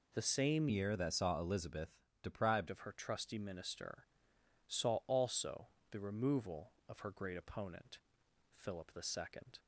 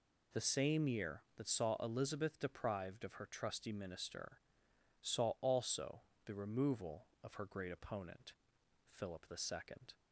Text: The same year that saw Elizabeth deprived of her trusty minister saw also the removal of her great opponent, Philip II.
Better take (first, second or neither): second